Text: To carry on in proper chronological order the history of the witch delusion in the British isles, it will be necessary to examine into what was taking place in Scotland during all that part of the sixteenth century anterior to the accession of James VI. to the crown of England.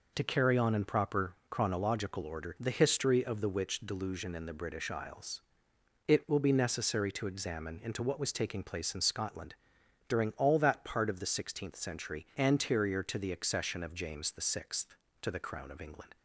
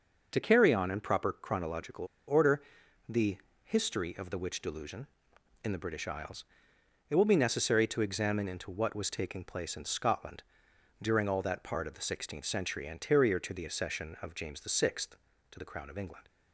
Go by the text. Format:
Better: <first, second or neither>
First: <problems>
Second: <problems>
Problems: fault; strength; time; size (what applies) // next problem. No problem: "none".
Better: first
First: pauses between "Scotland" and "during"; noticeable; at 9.5 s; 0.52 s long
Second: starts louder than the rest; noticeable; until 1.3 s; 6 dB // pauses between "chronological" and "order"; slight; at 2.0 s; 0.22 s long // pauses between "order" and "the"; at 2.6 s; 0.44 s long // pauses between "the" and "history"; slight; at 3.3 s; 0.26 s long // pauses between "Scotland" and "during"; noticeable; at 10.4 s; 0.58 s long